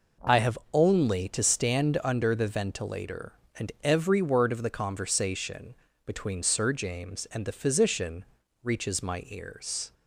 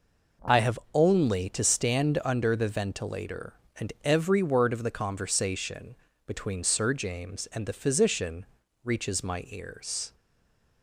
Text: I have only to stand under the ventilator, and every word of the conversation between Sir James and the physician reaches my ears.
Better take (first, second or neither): first